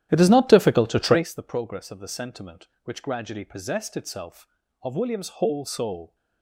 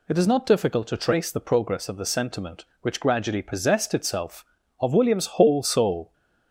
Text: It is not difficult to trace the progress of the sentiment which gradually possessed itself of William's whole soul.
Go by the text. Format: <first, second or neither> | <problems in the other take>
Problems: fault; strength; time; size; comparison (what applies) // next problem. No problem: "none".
second | starts louder than the rest; strong; until 1.3 s; 11.5 dB